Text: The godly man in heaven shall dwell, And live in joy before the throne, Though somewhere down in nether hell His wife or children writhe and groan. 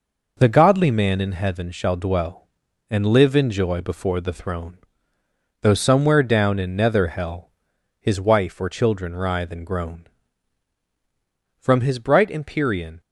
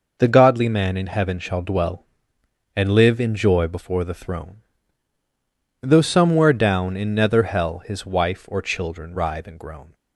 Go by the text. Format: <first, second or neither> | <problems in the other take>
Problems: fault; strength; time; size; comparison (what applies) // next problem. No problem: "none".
second | pauses between "hell" and "His"; noticeable; at 7.4 s; 0.50 s long // goes on to say "From his bright Empyrean"; from 11.6 s on; 1.3 s long